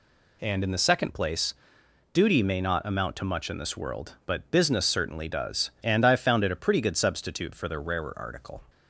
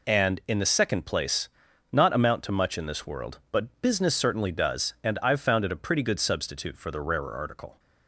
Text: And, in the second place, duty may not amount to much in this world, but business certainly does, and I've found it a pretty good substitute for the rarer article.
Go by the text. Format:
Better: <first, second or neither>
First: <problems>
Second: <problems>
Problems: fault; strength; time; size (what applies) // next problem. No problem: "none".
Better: first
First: none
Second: skips "duty may"; at 1.7 s